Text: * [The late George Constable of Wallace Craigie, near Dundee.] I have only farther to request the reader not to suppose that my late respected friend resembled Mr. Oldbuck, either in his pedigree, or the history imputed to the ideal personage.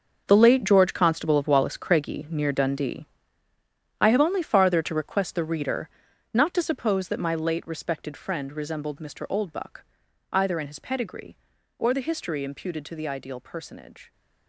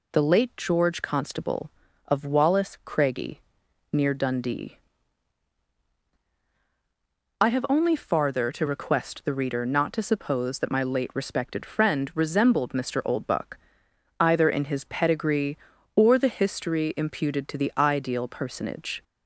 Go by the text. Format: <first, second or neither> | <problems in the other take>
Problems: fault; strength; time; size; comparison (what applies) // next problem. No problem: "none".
second | gets quieter; strong; throughout; 13 dB // pauses between "reader" and "not"; at 5.8 s; 0.44 s long